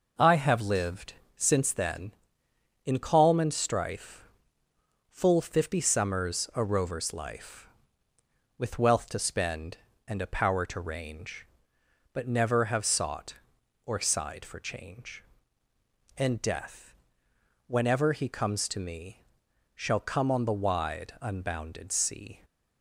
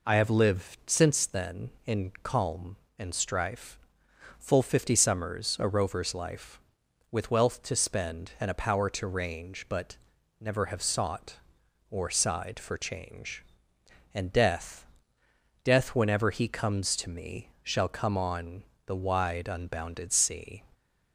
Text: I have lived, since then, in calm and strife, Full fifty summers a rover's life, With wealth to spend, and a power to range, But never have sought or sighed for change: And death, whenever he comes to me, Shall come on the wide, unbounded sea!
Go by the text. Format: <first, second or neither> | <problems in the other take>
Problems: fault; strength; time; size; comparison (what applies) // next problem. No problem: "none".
first | pauses between "But" and "never"; at 9.9 s; 0.42 s long // says "death" twice; at 15.6 s // pauses between "on" and "the"; slight; at 18.6 s; 0.24 s long